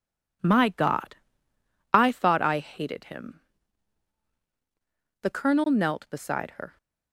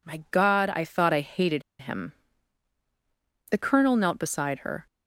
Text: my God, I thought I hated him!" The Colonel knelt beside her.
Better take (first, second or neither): first